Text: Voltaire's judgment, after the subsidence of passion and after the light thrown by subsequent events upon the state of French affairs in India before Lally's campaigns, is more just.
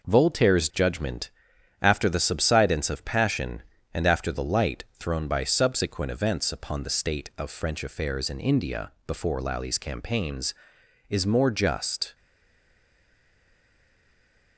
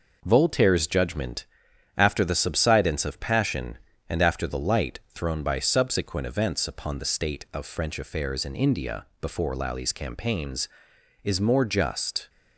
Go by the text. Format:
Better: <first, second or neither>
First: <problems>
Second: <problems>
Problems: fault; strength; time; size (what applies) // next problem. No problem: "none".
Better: second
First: pauses between "India" and "before"; slight; at 8.9 s; 0.16 s long // stays silent after the last word; from 12.1 s on; 2.4 s long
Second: pauses between "India" and "before"; slight; at 9.0 s; 0.16 s long